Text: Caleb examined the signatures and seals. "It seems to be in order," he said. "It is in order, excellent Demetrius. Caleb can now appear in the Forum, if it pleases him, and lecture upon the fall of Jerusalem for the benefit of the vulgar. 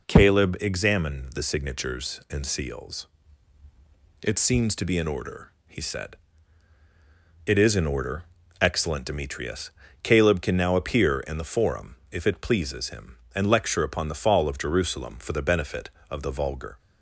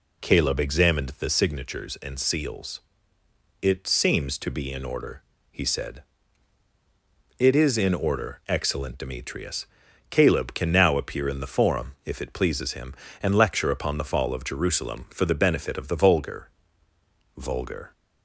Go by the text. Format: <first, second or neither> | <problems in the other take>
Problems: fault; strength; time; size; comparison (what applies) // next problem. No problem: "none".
first | says "vulgar" twice; at 17.3 s